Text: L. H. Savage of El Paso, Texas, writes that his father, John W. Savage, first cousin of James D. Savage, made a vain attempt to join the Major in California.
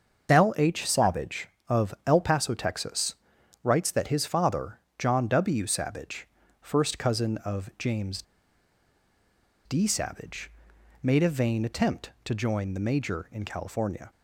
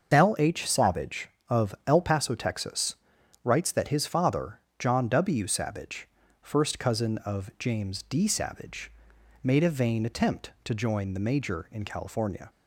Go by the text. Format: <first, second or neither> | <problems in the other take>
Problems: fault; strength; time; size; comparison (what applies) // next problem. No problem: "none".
second | starts louder than the rest; until 1.3 s; 6.5 dB; also in the second // pauses between "James" and "D"; strong; at 8.2 s; 1.4 s long